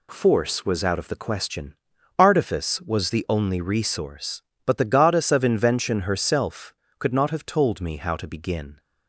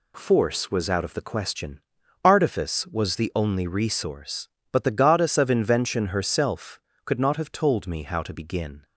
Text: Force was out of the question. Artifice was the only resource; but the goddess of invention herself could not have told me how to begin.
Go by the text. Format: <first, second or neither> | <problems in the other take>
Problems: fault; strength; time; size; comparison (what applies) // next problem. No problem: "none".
neither | none